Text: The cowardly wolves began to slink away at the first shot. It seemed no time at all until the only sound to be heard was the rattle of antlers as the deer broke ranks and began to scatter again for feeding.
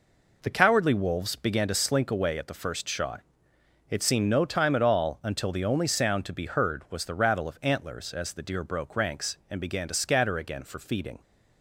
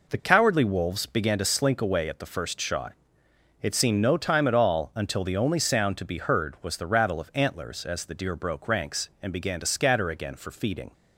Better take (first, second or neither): neither